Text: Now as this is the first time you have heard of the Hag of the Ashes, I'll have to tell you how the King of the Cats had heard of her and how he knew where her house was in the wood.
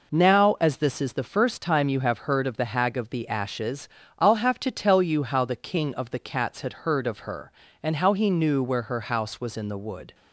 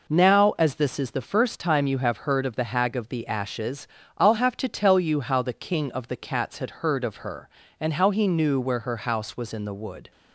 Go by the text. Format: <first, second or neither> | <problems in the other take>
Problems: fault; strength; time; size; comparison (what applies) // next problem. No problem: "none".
neither | none